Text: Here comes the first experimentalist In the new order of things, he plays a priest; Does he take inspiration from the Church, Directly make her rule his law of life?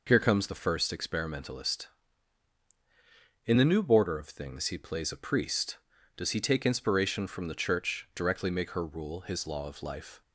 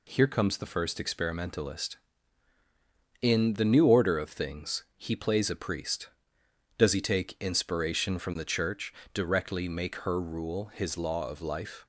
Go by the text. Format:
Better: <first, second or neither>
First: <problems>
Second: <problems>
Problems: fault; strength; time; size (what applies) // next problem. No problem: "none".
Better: second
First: says "border" for "order"; at 3.8 s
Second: none